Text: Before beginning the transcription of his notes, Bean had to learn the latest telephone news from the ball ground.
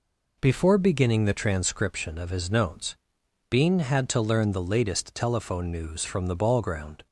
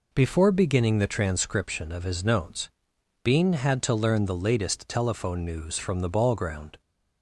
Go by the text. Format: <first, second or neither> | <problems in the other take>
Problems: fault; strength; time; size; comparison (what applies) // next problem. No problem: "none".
neither | none